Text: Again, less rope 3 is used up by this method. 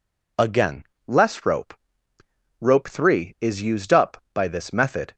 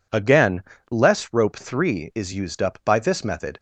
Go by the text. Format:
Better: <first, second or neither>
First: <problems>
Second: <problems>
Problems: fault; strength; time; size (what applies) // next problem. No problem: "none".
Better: second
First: says "rope" twice; at 2.5 s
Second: none